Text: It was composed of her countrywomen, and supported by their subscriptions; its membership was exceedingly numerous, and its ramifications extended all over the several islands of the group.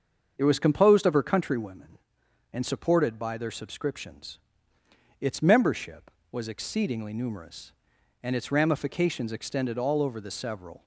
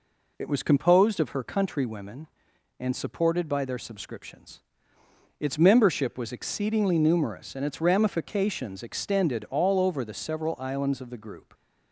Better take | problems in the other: second | starts louder than the rest; until 1.3 s; 7 dB // stops before "islands of the group"; at 10.8 s

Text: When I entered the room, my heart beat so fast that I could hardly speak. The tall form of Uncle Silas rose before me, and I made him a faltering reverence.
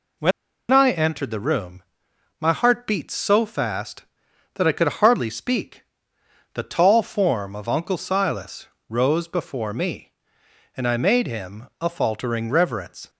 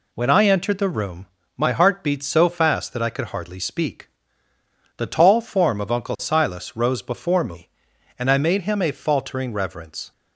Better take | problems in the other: second | pauses between "When" and "I"; at 0.3 s; 0.40 s long // pauses between "Silas" and "rose"; slight; at 8.6 s; 0.22 s long

